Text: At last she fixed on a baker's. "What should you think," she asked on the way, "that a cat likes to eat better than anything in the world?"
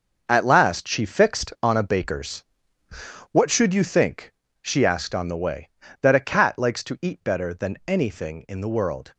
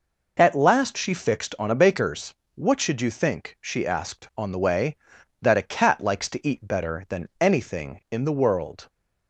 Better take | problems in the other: second | gets quieter; strong; throughout; 10.5 dB

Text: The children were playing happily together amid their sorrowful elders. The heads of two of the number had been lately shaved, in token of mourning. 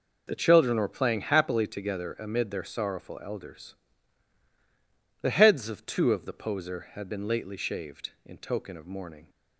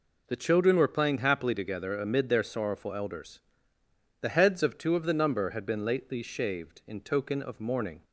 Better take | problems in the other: second | says "poser" for "number"; at 6.3 s

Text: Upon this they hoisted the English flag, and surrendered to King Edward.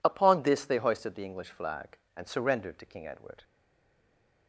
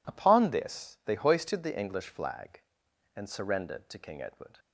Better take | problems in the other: second | stays silent after the last word; from 3.4 s on; 1.0 s long

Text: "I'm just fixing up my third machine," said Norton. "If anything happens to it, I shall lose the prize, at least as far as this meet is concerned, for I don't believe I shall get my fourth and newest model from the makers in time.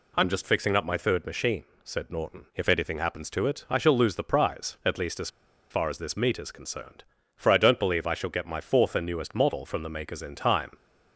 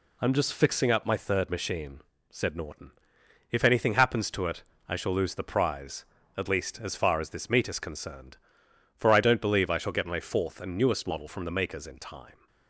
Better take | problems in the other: second | pauses between "as" and "far"; at 5.2 s; 0.41 s long

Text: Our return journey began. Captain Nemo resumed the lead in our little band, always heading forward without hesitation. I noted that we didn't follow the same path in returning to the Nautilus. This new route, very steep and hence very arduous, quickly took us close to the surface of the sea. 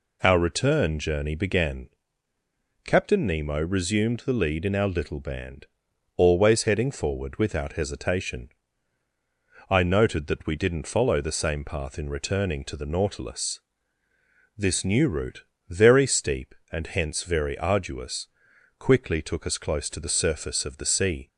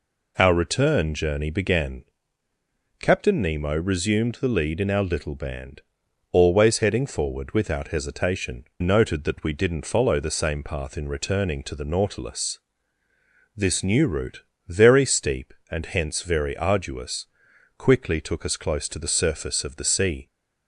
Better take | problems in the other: first | skips "I"; at 8.7 s

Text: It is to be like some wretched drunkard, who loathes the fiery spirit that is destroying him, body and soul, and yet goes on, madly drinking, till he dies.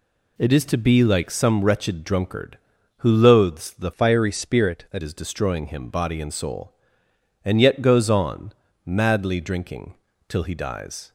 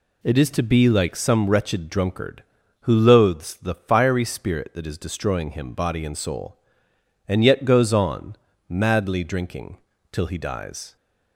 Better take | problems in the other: second | changes voice from "fiery" to "that"; from 3.9 to 5.0 s; 1.1 s long

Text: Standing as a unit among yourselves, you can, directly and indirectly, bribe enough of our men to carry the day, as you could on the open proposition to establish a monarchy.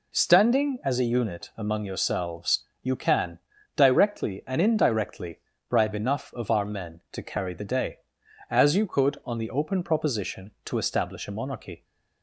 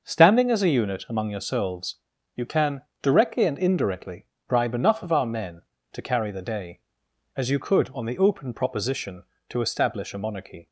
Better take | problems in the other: neither | none

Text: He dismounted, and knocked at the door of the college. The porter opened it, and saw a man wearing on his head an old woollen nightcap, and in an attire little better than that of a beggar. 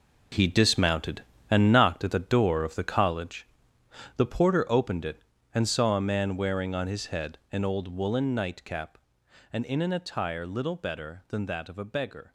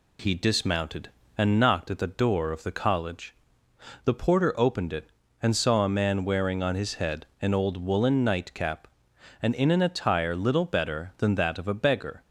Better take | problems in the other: second | gets quieter; strong; throughout; 11.5 dB

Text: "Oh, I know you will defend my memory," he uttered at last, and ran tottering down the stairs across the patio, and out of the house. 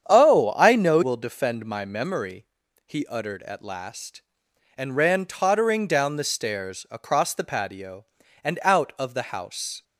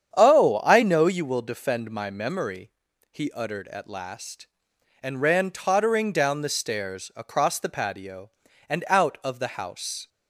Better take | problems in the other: second | starts louder than the rest; strong; until 1.1 s; 8.5 dB; strong in the second // skips "you"; at 1.0 s

